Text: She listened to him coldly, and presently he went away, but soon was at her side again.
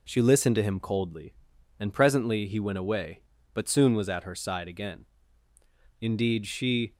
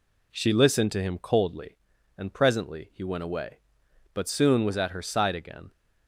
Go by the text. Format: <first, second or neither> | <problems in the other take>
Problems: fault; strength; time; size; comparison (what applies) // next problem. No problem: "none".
second | goes on to say "Indeed she"; noticeable; from 5.9 s on; 0.94 s long